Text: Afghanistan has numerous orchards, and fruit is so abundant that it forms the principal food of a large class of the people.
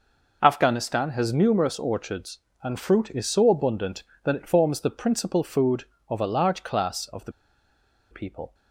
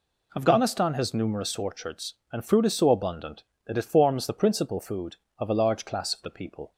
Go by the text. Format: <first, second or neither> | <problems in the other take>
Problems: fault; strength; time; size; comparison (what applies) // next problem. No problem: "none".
second | pauses between "the" and "people"; noticeable; at 7.3 s; 0.79 s long